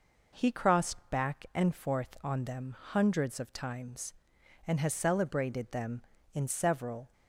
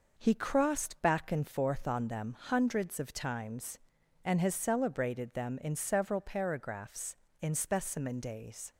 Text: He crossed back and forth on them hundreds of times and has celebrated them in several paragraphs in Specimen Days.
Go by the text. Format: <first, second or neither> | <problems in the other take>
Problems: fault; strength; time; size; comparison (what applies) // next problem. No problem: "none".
second | stops before "paragraphs in Specimen Days"; at 7.1 s